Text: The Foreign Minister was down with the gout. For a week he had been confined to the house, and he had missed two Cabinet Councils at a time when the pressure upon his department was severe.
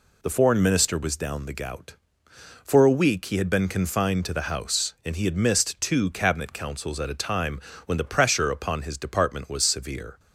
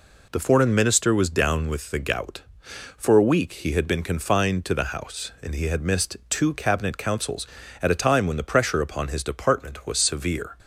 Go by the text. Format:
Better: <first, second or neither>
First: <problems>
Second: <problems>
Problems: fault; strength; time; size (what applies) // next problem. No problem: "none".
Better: second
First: skips "with"; at 1.4 s // pauses between "time" and "when"; slight; at 7.5 s; 0.28 s long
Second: none